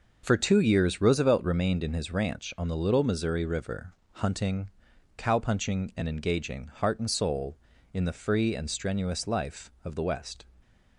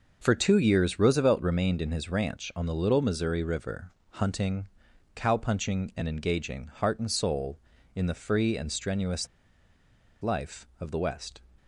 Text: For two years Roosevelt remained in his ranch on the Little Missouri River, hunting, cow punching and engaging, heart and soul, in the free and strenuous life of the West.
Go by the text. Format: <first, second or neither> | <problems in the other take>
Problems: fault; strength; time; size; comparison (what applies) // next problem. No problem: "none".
first | pauses between "strenuous" and "life"; noticeable; at 9.2 s; 0.95 s long